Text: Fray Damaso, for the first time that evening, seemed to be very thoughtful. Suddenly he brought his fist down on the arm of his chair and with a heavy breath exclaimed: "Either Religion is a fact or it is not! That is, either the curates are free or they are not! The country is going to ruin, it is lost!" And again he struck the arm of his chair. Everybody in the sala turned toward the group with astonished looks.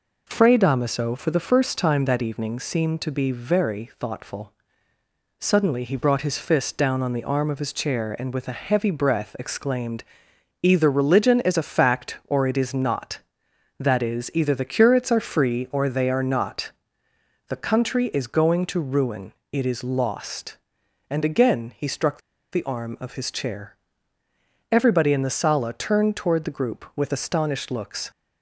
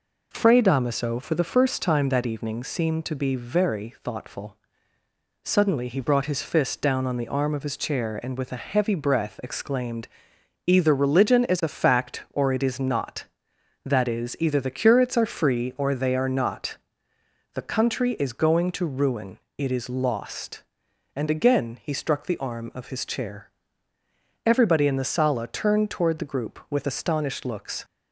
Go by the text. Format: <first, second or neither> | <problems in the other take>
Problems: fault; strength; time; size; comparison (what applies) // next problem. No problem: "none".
second | pauses between "struck" and "the"; slight; at 22.2 s; 0.31 s long